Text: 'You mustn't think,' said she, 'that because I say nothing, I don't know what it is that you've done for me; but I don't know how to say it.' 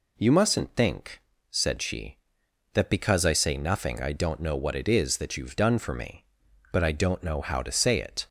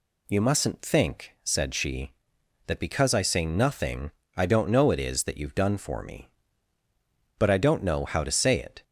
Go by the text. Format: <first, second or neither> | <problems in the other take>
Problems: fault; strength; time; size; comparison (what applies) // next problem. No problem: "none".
first | skips "what"; at 4.9 s